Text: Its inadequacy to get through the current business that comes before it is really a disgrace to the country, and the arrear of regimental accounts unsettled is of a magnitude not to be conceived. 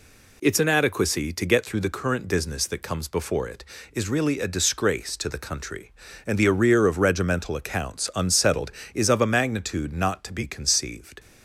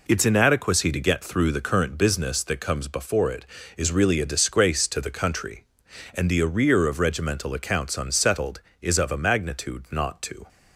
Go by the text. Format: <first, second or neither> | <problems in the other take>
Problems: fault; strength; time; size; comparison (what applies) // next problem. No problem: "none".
first | stops before "be conceived"; at 10.4 s